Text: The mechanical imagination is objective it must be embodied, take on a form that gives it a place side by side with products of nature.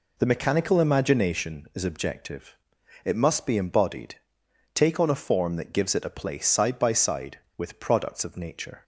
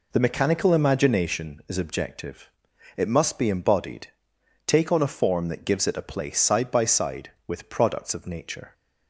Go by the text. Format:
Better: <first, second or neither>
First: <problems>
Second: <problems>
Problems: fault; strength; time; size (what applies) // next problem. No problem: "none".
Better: neither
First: pauses between "objective" and "it"; noticeable; at 2.5 s; 0.50 s long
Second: pauses between "objective" and "it"; noticeable; at 2.4 s; 0.48 s long